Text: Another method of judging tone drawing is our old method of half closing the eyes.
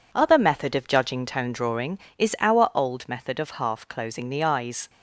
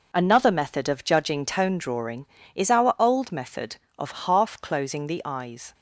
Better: second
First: says "Other" for "Another"; at 0.1 s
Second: none

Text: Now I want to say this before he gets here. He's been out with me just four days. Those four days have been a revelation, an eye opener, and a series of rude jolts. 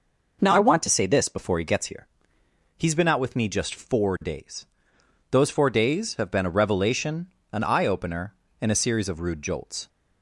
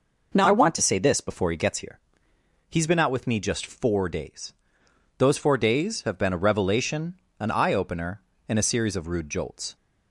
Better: neither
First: none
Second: none

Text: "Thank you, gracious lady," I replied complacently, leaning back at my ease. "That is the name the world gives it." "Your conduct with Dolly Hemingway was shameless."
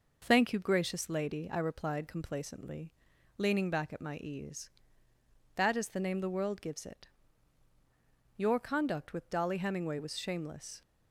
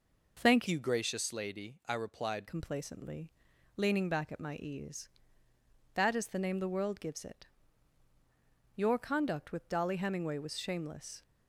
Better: first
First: none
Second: changes voice from "you" to "replied"; from 0.6 to 2.4 s; 1.8 s long

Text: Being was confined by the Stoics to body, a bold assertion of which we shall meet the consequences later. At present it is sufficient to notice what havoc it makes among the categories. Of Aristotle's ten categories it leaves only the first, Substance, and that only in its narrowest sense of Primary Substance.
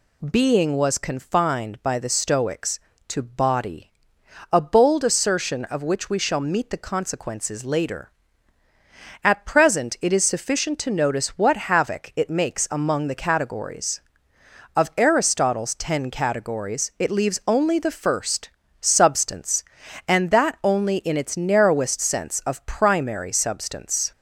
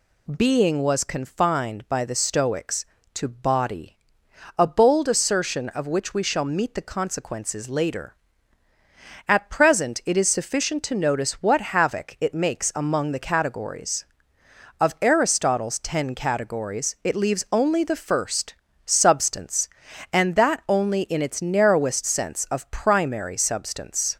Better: neither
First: none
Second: none

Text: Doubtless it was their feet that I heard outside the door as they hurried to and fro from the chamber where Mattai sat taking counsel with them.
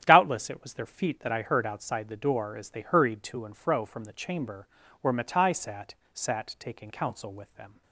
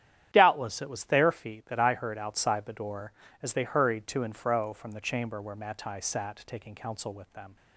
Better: second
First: starts louder than the rest; strong; until 1.0 s; 10 dB // pauses between "chamber" and "where"; slight; at 4.6 s; 0.34 s long // says "sat" twice; at 6.1 s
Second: starts louder than the rest; strong; until 1.3 s; 10.5 dB

